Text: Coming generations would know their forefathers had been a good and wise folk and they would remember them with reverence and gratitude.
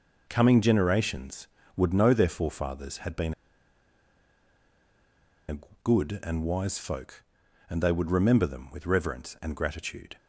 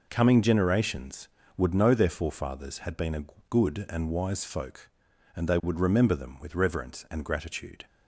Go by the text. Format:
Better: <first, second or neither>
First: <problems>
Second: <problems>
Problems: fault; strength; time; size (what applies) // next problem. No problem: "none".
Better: second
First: pauses between "been" and "a"; strong; at 3.3 s; 2.1 s long // pauses between "a" and "good"; slight; at 5.5 s; 0.26 s long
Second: pauses between "a" and "good"; slight; at 3.2 s; 0.26 s long